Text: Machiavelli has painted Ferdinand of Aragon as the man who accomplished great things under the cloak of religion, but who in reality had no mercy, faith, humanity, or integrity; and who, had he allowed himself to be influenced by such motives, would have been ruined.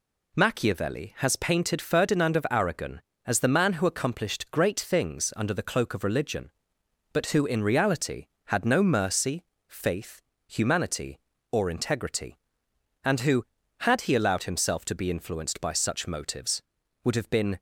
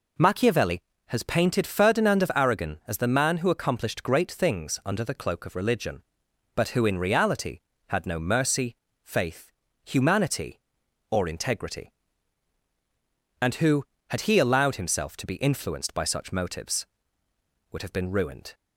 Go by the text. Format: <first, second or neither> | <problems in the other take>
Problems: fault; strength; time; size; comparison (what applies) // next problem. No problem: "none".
second | stops before "ruined"; at 17.5 s